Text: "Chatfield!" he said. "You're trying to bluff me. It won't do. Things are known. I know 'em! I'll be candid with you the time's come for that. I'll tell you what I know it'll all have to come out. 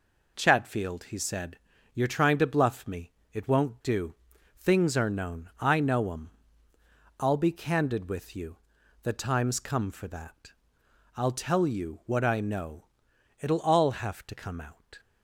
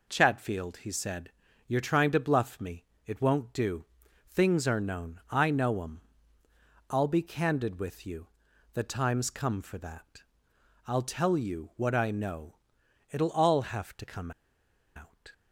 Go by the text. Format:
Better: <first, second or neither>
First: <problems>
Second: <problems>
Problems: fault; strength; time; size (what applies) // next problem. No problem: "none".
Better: first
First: pauses between "you" and "the"; at 8.5 s; 0.44 s long // pauses between "know" and "it'll"; noticeable; at 12.8 s; 0.54 s long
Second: pauses between "you" and "the"; at 8.2 s; 0.44 s long // pauses between "know" and "it'll"; noticeable; at 12.5 s; 0.54 s long // pauses between "come" and "out"; noticeable; at 14.3 s; 0.65 s long